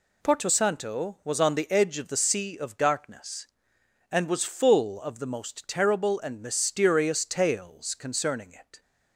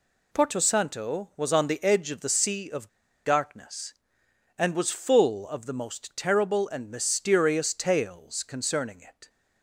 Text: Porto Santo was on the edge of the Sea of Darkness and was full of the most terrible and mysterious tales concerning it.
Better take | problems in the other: first | pauses between "of" and "Darkness"; at 2.8 s; 0.36 s long

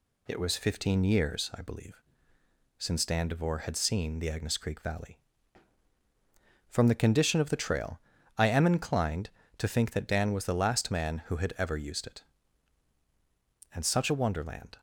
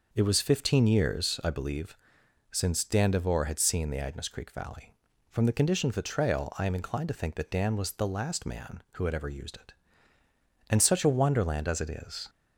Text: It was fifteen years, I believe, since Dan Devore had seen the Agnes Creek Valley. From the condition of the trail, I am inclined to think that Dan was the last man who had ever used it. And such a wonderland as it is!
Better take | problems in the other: second | stops before "as it is"; at 14.7 s

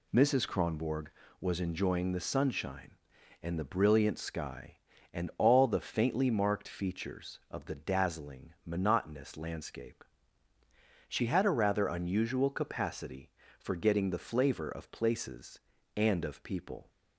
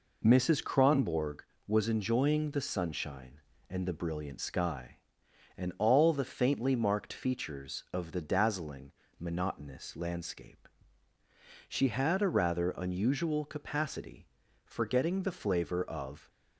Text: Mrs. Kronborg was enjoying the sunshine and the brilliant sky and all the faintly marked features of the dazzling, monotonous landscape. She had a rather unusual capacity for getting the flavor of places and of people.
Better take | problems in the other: first | stops before "places and of people"; at 16.2 s

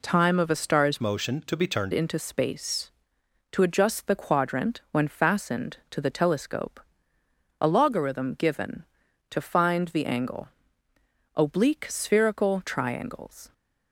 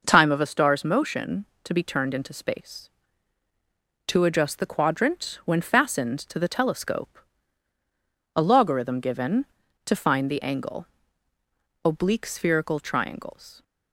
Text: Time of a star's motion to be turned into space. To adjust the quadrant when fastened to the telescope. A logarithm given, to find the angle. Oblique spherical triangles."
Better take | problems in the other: second | changes voice from "motion" to "turned"; from 1.0 to 1.9 s; 0.9 s long

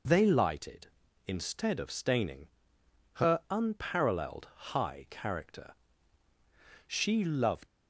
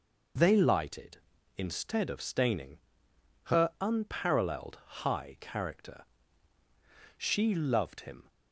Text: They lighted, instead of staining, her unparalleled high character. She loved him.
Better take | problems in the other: second | stops before "him"; at 7.6 s

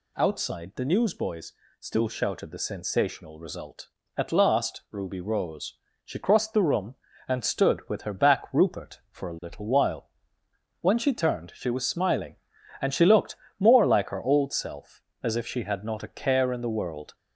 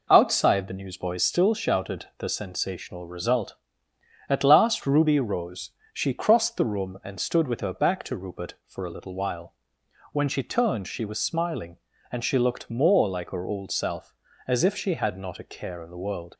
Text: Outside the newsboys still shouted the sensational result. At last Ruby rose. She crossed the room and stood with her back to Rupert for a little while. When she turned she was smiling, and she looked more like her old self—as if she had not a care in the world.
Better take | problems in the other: second | pauses between "newsboys" and "still"; slight; at 1.5 s; 0.26 s long // skips "to"; at 8.4 s // pauses between "looked" and "more"; slight; at 13.3 s; 0.22 s long

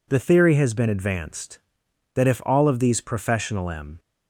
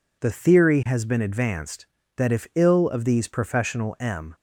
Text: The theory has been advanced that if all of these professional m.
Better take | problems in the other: first | says "ill" for "all"; at 2.5 s

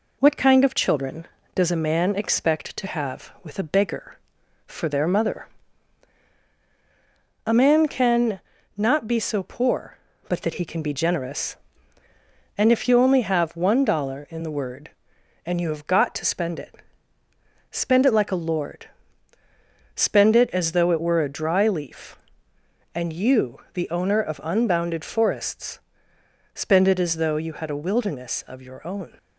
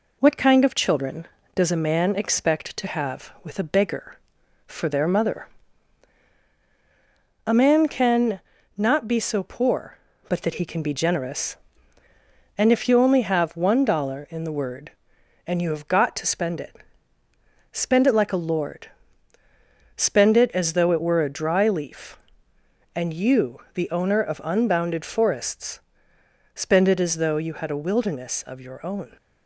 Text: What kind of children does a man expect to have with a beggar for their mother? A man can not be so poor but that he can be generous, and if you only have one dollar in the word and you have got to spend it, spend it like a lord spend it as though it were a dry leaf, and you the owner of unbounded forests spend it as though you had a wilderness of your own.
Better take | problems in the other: neither | pauses between "can" and "not"; slight; the same in both // pauses between "lord" and "spend"; the same in both // pauses between "forests" and "spend"; noticeable; the same in both

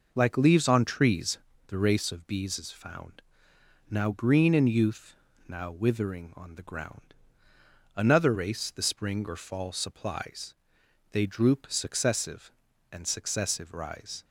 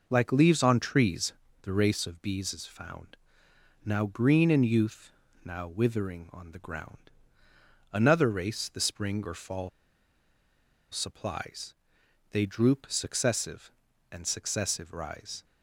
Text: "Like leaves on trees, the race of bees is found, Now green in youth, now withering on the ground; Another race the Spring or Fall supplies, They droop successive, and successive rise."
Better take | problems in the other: first | pauses between "Fall" and "supplies"; at 9.6 s; 1.2 s long

